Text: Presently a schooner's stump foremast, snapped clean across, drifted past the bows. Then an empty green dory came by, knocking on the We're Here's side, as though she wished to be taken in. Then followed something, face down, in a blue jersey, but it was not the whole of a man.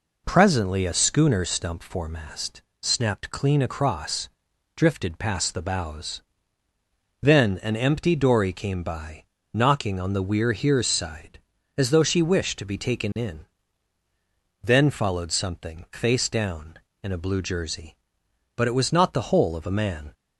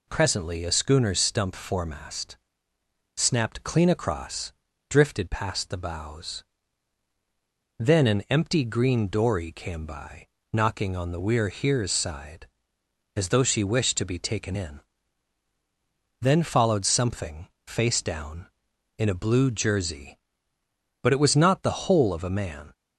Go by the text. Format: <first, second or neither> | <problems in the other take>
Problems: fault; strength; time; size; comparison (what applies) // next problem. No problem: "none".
second | skips "green"; at 8.1 s